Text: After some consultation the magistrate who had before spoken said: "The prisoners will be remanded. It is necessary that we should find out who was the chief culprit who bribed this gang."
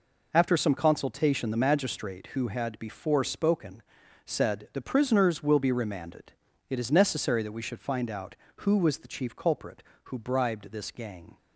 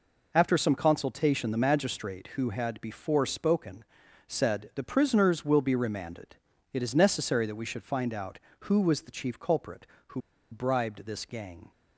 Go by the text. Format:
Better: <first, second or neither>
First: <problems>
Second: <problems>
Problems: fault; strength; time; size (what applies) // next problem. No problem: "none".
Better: first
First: pauses between "spoken" and "said"; at 3.8 s; 0.44 s long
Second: pauses between "spoken" and "said"; at 3.8 s; 0.44 s long // pauses between "who" and "bribed"; slight; at 10.2 s; 0.31 s long